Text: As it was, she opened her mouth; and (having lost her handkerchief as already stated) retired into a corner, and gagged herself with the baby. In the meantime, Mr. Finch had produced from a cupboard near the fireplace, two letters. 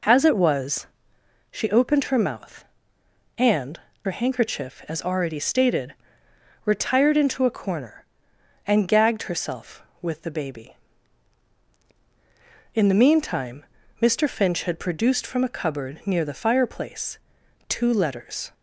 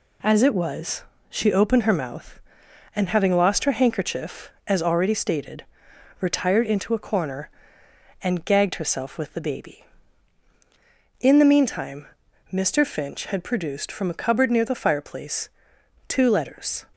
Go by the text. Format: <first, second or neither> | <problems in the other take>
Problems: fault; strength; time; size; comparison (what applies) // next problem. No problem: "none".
second | skips "having lost"; at 3.9 s